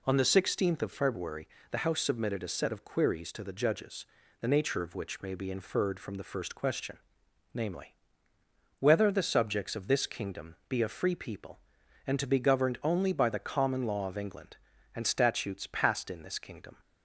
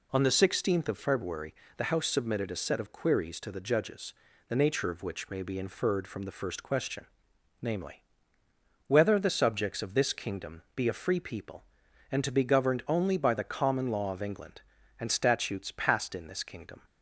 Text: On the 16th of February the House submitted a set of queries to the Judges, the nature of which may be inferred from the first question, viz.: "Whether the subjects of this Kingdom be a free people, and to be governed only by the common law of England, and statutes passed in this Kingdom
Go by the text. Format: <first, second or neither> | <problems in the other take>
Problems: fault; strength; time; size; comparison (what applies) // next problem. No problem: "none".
neither | pauses between "February" and "the"; slight; the same in both